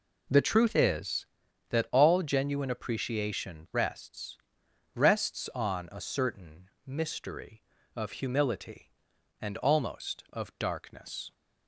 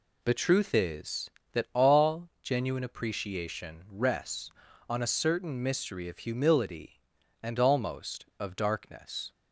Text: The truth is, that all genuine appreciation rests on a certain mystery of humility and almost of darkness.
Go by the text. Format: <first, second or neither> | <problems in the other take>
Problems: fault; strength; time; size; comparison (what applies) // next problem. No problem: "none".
second | says "rests" twice; at 4.9 s // pauses between "certain" and "mystery"; slight; at 6.6 s; 0.18 s long